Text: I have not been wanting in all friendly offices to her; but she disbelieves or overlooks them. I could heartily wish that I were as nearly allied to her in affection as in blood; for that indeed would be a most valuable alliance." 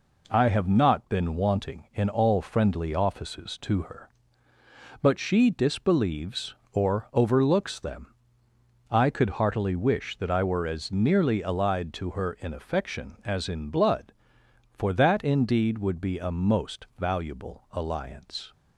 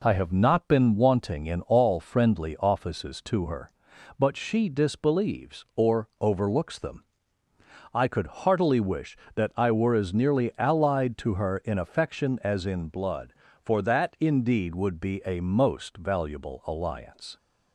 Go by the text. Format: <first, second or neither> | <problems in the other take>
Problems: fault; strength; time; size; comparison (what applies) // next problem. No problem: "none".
neither | none